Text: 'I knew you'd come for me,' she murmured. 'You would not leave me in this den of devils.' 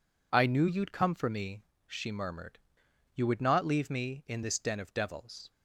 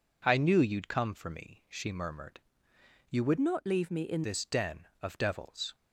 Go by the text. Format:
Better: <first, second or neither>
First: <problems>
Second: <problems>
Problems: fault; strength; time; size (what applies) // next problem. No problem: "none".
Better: first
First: none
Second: changes voice from "not" to "in"; from 3.4 to 4.2 s; 0.8 s long